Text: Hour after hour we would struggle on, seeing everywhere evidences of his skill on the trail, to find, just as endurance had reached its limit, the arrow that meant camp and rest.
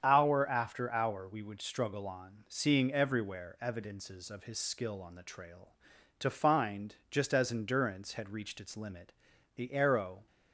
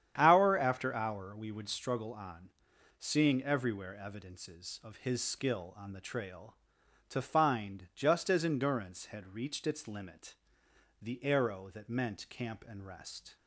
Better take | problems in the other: second | starts louder than the rest; strong; until 1.0 s; 8 dB; strong in the second // stops before "that meant camp and rest"; at 10.2 s

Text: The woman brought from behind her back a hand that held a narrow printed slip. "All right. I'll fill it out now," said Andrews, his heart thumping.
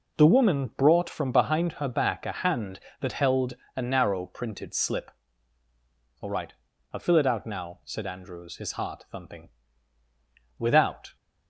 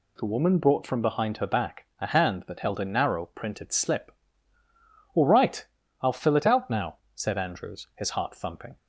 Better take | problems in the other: second | pauses between "held" and "a"; slight; at 3.5 s; 0.22 s long // goes on to say "Without"; from 10.5 s on; 0.56 s long

